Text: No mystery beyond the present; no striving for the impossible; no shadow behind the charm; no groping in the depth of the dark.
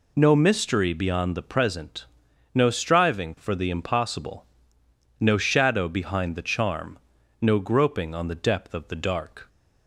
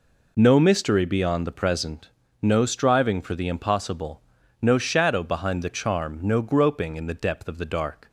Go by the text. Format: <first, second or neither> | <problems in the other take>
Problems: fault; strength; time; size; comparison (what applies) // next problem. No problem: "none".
second | says "on" for "in"; at 8.1 s